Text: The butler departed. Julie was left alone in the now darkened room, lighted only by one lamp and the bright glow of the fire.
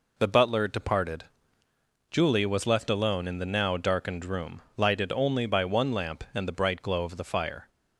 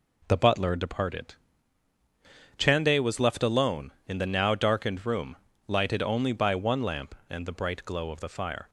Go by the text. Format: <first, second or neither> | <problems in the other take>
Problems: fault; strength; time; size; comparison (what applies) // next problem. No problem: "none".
first | says "Chande" for "Julie"; at 2.5 s